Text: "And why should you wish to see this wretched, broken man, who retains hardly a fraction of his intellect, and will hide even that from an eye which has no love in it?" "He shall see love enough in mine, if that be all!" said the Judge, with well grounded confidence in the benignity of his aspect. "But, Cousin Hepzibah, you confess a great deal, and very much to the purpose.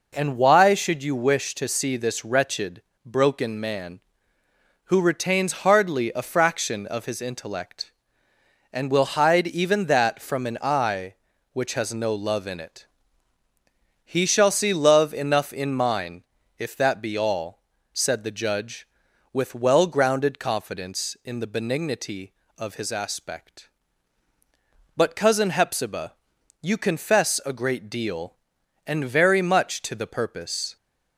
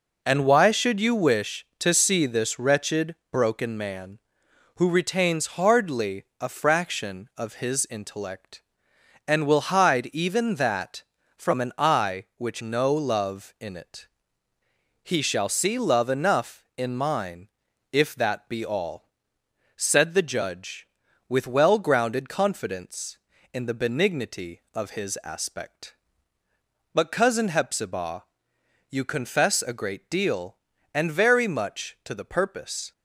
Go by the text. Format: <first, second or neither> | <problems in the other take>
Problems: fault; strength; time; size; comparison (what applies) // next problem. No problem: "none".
first | pauses between "hardly" and "a"; slight; at 6.2 s; 0.16 s long // skips "has"; at 12.6 s